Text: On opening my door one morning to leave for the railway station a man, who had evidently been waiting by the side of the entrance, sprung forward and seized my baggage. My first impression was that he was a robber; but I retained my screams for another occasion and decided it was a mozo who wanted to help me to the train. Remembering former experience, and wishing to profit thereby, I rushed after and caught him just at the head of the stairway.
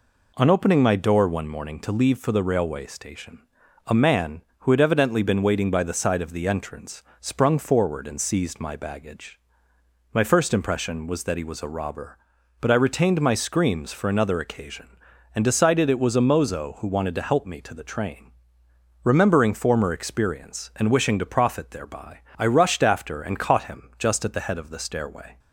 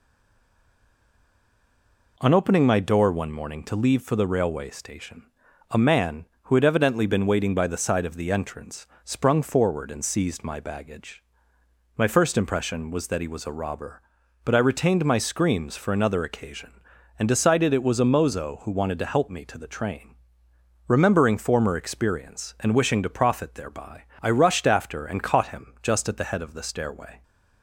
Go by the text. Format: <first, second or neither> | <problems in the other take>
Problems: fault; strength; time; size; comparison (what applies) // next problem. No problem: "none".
first | stays silent before the first word; until 2.1 s; 2.1 s long // pauses between "station" and "a"; noticeable; at 5.2 s; 0.46 s long; noticeable in the first